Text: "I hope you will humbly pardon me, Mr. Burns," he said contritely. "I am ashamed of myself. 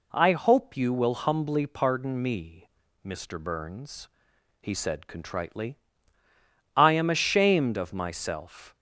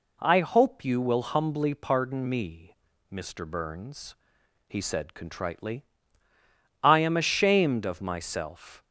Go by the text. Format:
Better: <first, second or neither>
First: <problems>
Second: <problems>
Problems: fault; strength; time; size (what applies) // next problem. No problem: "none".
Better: neither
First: none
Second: none